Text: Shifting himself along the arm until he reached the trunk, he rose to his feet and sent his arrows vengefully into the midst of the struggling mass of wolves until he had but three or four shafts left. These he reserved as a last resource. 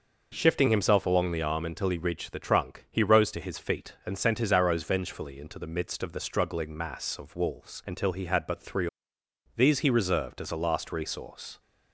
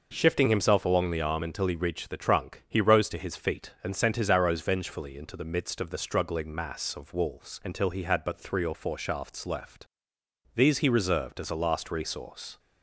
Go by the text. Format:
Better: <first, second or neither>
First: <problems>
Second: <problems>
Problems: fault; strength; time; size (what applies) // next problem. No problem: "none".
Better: second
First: skips "or four shafts left"; at 9.2 s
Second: none